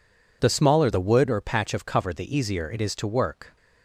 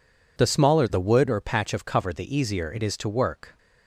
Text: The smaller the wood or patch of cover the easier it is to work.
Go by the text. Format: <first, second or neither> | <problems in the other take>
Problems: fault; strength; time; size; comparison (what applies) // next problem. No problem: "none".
neither | none